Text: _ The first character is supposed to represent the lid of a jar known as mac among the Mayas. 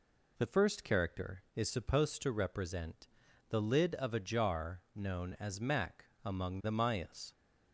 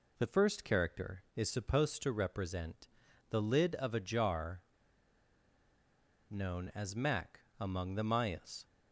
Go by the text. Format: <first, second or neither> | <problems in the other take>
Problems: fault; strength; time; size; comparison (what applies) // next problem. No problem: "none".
first | pauses between "represent" and "the"; at 2.8 s; 0.42 s long; also in the first // pauses between "jar" and "known"; strong; at 4.6 s; 1.6 s long // pauses between "mac" and "among"; slight; at 7.4 s; 0.20 s long; slight in the first